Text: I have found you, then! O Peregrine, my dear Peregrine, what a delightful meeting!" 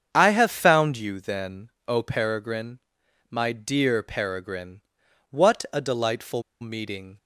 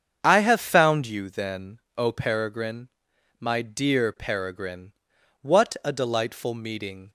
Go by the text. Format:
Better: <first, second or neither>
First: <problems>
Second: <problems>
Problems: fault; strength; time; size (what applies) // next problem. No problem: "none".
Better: second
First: starts louder than the rest; strong; until 1.1 s; 7.5 dB // pauses between "delightful" and "meeting"; slight; at 6.4 s; 0.19 s long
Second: starts louder than the rest; strong; until 1.2 s; 7.5 dB